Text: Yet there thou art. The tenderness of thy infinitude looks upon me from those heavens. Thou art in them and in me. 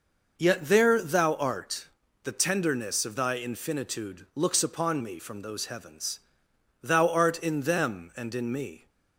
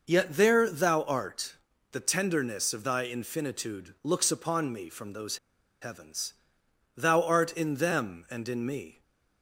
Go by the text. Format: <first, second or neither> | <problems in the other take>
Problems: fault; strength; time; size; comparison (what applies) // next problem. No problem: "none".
first | pauses between "those" and "heavens"; at 5.3 s; 0.43 s long // stays silent after the last word; slight; from 8.9 s on; 0.5 s long